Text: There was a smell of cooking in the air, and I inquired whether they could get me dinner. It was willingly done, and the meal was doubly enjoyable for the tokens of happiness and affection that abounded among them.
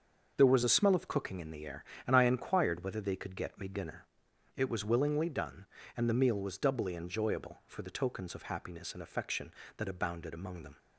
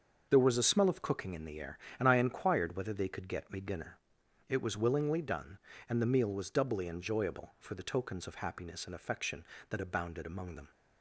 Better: neither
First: starts louder than the rest; until 1.3 s; 6.5 dB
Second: starts louder than the rest; until 1.3 s; 6.5 dB

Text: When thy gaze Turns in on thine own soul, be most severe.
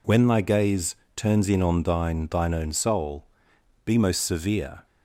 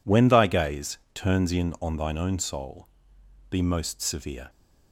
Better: second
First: pauses between "gaze" and "Turns"; slight; at 0.9 s; 0.20 s long // says "thine" twice; at 2.2 s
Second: pauses between "gaze" and "Turns"; slight; at 0.9 s; 0.16 s long

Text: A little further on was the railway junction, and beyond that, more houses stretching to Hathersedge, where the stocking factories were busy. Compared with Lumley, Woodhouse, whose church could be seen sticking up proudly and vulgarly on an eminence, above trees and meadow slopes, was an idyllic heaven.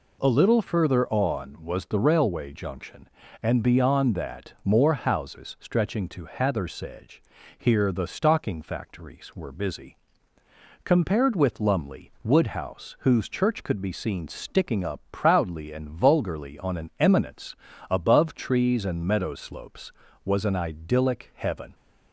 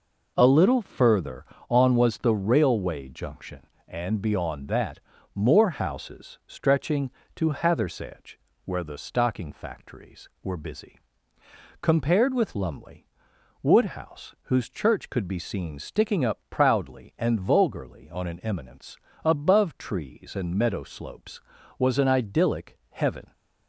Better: second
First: says "here" for "where"; at 7.5 s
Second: none

